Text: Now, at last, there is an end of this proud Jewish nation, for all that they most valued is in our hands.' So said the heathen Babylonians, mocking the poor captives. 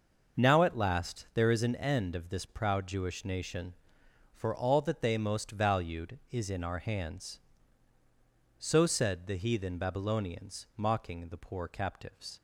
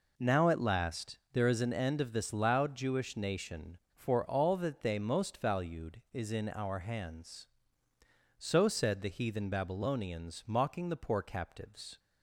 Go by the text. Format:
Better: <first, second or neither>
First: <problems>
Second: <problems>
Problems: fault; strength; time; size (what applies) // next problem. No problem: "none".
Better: first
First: none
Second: says "loud" for "proud"; at 2.3 s